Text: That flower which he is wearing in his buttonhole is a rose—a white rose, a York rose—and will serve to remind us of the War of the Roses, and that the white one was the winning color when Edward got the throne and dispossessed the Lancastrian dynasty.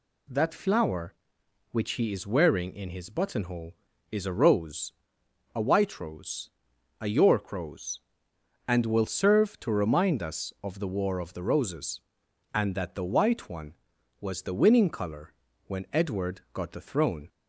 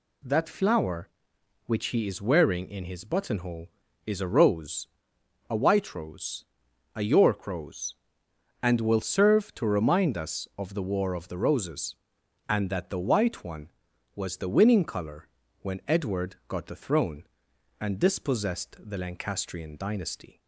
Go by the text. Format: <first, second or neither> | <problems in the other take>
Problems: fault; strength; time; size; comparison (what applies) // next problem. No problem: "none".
second | pauses between "color" and "when"; slight; at 15.3 s; 0.34 s long; slight in the second // stops before "and dispossessed the Lancastrian dynasty"; at 17.2 s